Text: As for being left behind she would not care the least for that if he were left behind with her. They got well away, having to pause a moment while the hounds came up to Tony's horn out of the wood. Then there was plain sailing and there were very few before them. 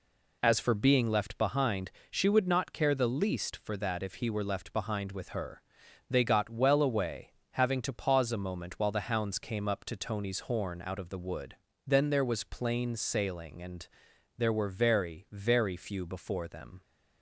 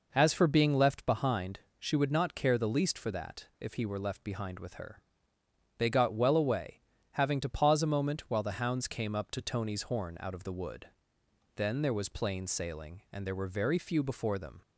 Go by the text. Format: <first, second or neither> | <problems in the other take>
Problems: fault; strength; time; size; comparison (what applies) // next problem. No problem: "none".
second | pauses between "behind" and "she"; slight; at 1.9 s; 0.20 s long; slight in the second // pauses between "and" and "there"; noticeable; at 13.8 s; 0.50 s long // says "very" twice; at 15.3 s